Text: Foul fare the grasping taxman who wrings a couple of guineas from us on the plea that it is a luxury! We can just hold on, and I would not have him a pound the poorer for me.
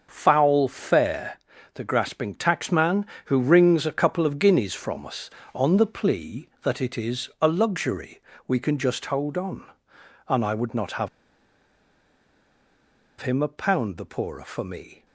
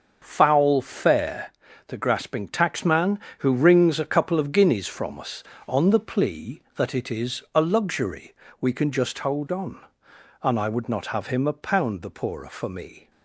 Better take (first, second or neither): second